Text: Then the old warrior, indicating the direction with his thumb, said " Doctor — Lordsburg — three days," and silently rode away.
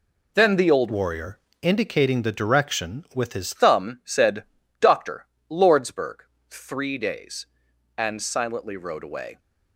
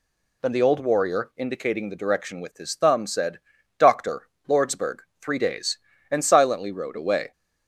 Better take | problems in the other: second | changes voice from "warrior" to "his"; from 0.8 to 3.5 s; 2.7 s long

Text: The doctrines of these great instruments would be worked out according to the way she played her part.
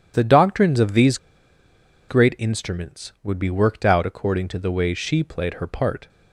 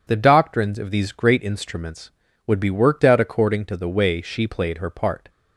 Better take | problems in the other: second | pauses between "these" and "great"; noticeable; at 1.1 s; 0.91 s long

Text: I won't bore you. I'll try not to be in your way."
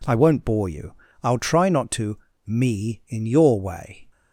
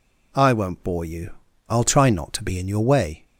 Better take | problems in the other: second | says "me" for "be"; at 2.4 s

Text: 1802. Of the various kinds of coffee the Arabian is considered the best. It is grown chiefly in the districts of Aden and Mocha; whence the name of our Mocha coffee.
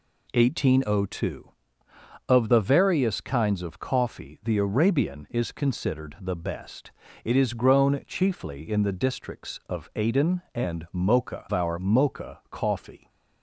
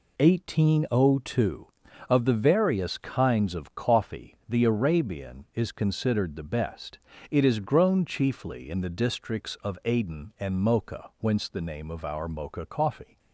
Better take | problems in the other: second | skips "whence the name of"; at 11.4 s

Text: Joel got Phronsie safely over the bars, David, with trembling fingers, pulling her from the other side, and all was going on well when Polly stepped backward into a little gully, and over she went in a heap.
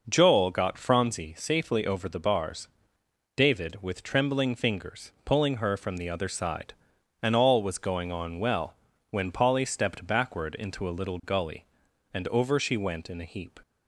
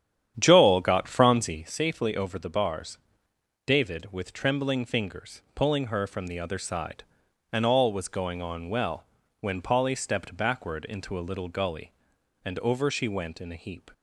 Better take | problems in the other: first | starts louder than the rest; strong; until 1.8 s; 9.5 dB // pauses between "well" and "when"; at 9.0 s; 0.38 s long; also in the first

